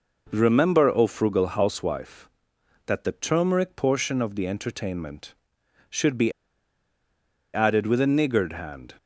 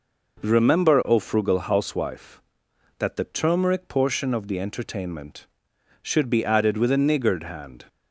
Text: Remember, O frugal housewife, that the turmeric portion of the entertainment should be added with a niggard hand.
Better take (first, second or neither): second